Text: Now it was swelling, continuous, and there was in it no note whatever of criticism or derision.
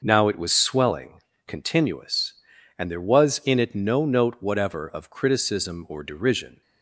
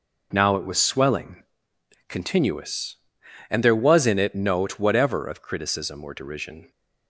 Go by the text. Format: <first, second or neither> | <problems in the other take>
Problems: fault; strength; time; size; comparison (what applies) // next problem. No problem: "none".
first | skips "no"; at 4.3 s